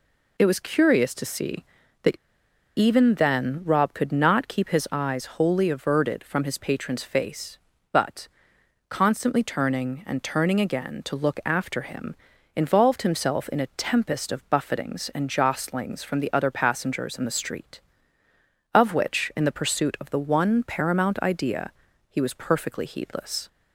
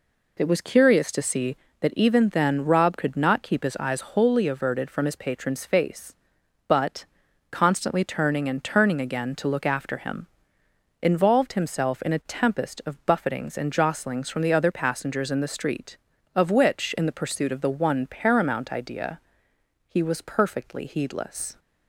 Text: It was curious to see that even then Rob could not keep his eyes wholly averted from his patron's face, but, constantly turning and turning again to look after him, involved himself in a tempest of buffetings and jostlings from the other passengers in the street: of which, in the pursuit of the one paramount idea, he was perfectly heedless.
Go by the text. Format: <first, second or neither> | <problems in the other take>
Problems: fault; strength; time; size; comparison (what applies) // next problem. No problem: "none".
second | pauses between "that" and "even"; noticeable; at 2.1 s; 0.61 s long